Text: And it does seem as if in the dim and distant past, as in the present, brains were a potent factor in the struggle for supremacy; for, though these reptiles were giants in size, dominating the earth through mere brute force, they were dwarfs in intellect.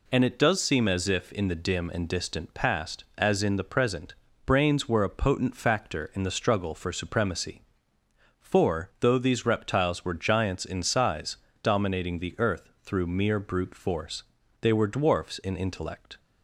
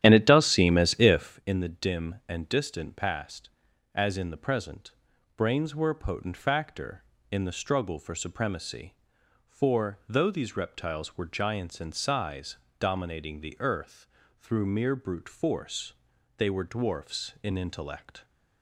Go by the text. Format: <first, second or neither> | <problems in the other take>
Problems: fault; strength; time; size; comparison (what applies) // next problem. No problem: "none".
first | starts louder than the rest; strong; until 1.4 s; 11.5 dB // pauses between "earth" and "through"; slight; at 14.0 s; 0.32 s long; slight in the first